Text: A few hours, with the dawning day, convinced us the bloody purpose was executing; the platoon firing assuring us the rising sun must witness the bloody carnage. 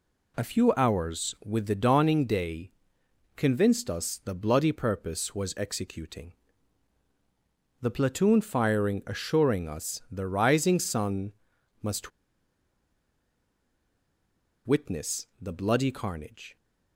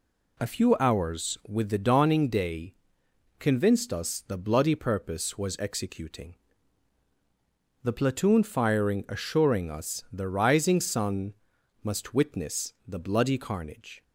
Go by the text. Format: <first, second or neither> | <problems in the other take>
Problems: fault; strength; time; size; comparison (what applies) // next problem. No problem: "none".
second | pauses between "sun" and "must"; noticeable; at 11.3 s; 0.48 s long; noticeable in the second // pauses between "must" and "witness"; strong; at 12.1 s; 2.5 s long